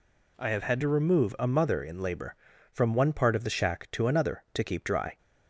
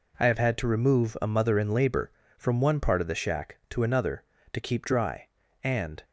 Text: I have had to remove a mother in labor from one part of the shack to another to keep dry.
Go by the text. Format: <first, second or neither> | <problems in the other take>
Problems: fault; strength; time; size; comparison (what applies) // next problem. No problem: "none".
first | goes on to say "And"; slight; from 5.6 s on; 0.40 s long